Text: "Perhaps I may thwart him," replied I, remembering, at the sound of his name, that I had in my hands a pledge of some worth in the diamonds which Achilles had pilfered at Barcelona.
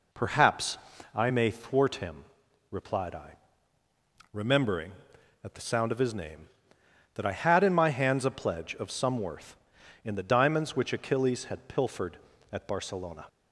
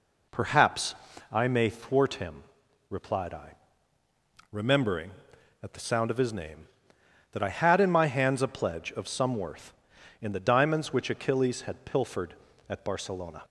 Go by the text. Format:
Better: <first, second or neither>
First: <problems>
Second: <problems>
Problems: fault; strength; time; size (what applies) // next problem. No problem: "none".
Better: neither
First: pauses between "Perhaps" and "I"; at 0.7 s; 0.38 s long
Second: pauses between "Perhaps" and "I"; at 0.9 s; 0.38 s long